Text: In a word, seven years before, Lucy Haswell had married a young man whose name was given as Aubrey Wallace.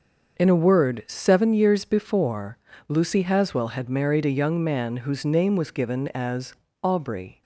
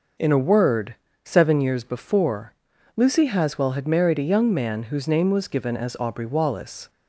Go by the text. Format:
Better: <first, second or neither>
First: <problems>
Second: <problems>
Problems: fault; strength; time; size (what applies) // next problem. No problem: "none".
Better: second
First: starts louder than the rest; until 1.4 s; 6.5 dB // pauses between "as" and "Aubrey"; slight; at 6.5 s; 0.30 s long // stops before "Wallace"; at 7.4 s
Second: none